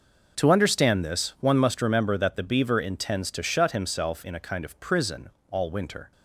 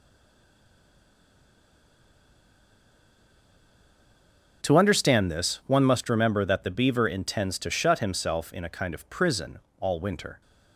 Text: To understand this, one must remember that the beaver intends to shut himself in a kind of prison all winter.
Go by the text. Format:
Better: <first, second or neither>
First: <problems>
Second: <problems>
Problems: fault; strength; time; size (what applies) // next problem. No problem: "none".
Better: first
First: pauses between "prison" and "all"; slight; at 5.2 s; 0.22 s long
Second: stays silent before the first word; strong; until 4.6 s; 4.6 s long // pauses between "prison" and "all"; slight; at 9.5 s; 0.22 s long